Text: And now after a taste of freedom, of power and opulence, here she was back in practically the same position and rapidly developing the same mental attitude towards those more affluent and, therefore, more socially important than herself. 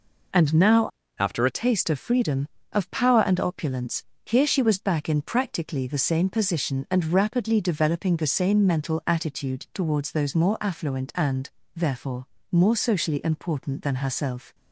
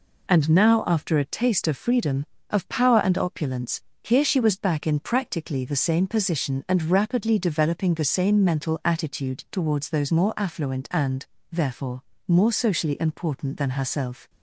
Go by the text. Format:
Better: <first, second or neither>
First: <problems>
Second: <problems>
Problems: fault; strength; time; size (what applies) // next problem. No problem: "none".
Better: second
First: changes voice from "after" to "a"; from 1.1 to 1.5 s; 0.4 s long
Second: none